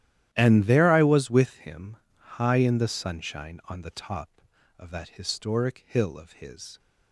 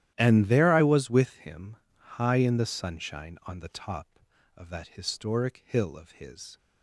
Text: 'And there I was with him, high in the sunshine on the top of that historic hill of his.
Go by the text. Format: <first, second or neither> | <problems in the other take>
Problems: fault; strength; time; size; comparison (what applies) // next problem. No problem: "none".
neither | starts louder than the rest; strong; the same in both